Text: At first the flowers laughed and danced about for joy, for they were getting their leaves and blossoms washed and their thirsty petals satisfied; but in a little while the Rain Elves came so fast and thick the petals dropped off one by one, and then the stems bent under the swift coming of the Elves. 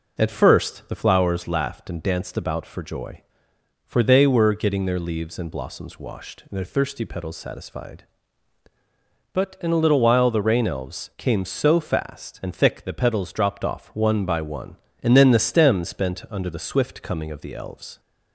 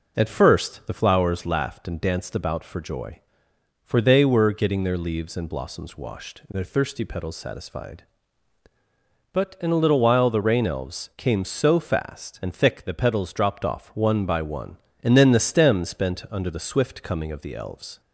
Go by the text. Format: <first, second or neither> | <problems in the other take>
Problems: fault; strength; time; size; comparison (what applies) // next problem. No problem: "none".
neither | none